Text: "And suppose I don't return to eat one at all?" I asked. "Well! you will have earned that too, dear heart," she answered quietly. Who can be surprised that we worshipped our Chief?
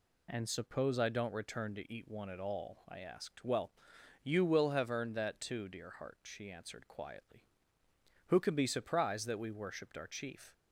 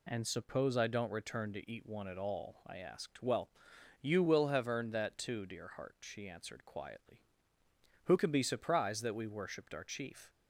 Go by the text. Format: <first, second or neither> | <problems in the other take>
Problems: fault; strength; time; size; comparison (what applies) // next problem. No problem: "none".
neither | none